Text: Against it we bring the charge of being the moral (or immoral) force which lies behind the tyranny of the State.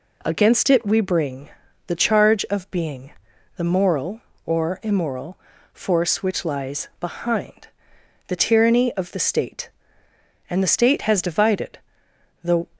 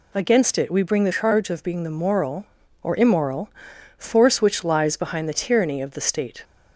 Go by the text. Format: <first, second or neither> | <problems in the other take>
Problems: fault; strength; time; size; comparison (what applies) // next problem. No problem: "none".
second | pauses between "bring" and "the"; at 1.4 s; 0.38 s long // pauses between "being" and "the"; at 3.1 s; 0.44 s long // pauses between "behind" and "the"; noticeable; at 7.6 s; 0.62 s long // goes on to say "And the State has divided the"; strong; from 10.4 s on; 2.2 s long